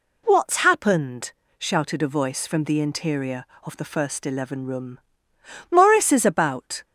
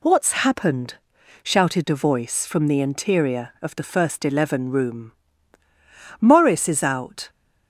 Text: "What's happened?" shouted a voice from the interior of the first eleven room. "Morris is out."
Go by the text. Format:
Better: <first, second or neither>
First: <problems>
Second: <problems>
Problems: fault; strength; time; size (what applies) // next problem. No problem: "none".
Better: second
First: says "about" for "out"; at 6.2 s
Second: none